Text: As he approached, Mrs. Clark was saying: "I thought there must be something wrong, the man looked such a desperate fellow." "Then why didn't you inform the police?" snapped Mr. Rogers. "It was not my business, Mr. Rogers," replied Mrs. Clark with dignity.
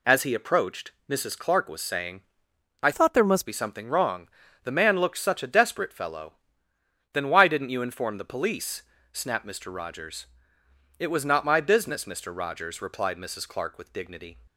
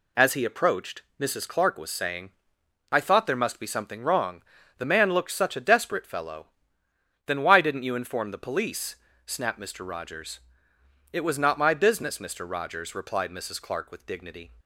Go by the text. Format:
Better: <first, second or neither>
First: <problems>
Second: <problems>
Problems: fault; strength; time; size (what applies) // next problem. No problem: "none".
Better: second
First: changes voice from "thought" to "must"; from 2.9 to 3.4 s; 0.5 s long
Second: none